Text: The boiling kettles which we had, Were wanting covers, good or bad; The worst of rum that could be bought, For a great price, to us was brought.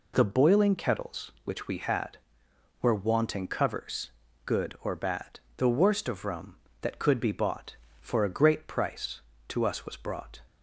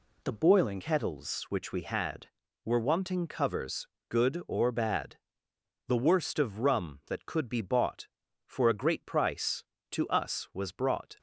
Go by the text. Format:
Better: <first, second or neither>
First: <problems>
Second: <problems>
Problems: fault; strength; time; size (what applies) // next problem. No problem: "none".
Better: first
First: none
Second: changes voice at "kettles"; from 0.8 s on; 10.3 s long